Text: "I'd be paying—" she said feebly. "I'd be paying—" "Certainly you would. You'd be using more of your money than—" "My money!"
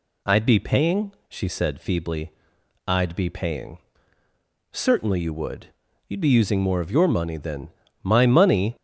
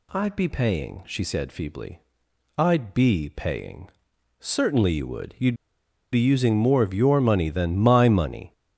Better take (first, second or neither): first